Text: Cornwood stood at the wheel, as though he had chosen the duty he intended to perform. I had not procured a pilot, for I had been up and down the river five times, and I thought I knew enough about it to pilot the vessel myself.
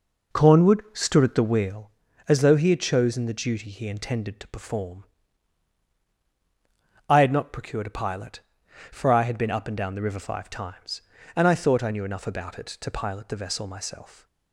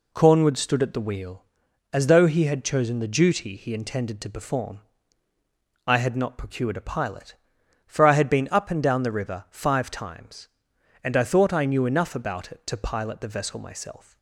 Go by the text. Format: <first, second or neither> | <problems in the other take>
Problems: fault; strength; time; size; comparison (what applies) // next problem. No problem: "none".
second | starts louder than the rest; noticeable; until 1.8 s; 5 dB